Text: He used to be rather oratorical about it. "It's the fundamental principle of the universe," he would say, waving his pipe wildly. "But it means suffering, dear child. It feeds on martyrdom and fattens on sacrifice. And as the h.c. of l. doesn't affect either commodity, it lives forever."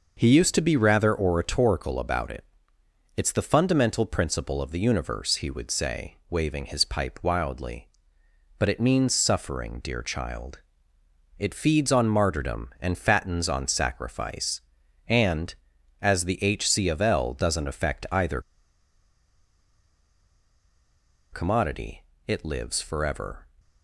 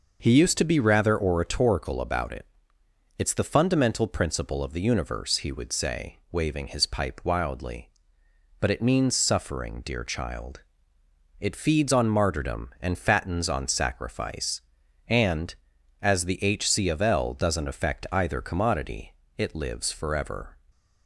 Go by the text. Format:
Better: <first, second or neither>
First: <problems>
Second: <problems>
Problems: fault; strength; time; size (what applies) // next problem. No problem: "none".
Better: second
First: pauses between "either" and "commodity"; strong; at 18.3 s; 2.9 s long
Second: none